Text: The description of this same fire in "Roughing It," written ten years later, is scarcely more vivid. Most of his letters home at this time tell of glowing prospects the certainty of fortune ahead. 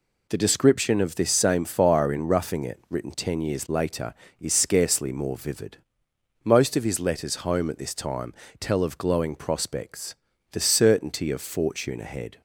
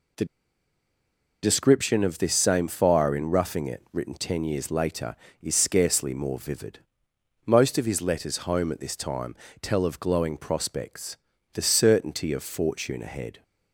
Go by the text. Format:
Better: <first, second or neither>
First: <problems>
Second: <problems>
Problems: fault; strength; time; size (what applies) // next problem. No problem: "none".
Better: first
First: pauses between "time" and "tell"; slight; at 8.3 s; 0.26 s long // pauses between "prospects" and "the"; slight; at 10.1 s; 0.36 s long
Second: pauses between "The" and "description"; at 0.2 s; 1.1 s long // pauses between "time" and "tell"; slight; at 9.3 s; 0.26 s long // pauses between "prospects" and "the"; slight; at 11.1 s; 0.36 s long